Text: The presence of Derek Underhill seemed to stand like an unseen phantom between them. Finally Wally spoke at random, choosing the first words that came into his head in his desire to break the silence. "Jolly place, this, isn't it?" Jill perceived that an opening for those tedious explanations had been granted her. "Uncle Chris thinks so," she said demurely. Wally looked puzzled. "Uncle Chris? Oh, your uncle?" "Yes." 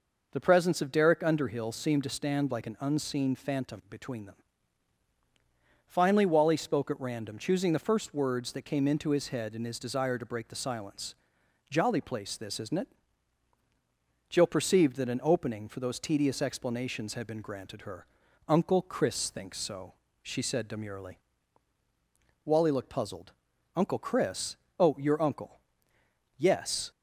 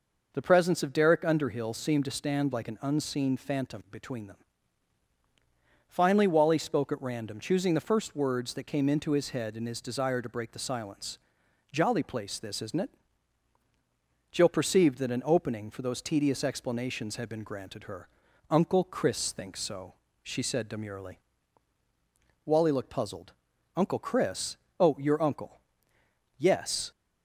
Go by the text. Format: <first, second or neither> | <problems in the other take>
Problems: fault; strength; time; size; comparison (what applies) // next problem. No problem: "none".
neither | none